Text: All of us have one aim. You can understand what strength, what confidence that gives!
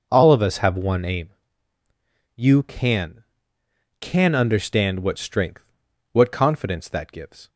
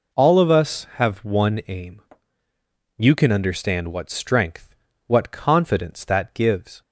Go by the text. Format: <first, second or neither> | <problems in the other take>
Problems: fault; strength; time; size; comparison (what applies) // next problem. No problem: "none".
second | says "can" twice; at 4.0 s